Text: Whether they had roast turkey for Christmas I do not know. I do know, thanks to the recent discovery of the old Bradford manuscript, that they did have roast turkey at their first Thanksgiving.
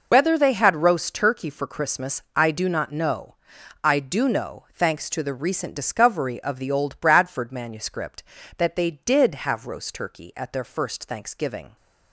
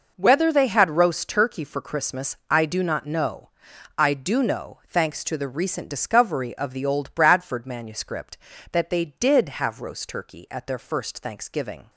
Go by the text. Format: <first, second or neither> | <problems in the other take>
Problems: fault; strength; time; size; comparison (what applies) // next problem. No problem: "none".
second | loses the start of "Whether"; at 0.1 s; 105 ms